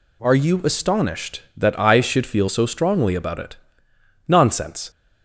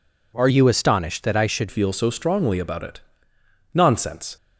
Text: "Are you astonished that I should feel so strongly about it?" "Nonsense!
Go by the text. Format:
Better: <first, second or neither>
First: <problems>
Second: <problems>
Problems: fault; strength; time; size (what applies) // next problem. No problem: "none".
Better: first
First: none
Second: changes voice from "you" to "should"; from 0.4 to 1.6 s; 1.2 s long